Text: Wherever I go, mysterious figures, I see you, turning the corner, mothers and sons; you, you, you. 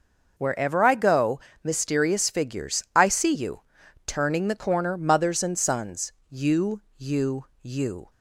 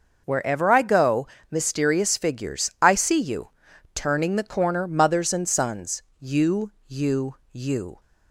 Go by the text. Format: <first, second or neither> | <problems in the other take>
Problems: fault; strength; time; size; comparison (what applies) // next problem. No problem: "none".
neither | none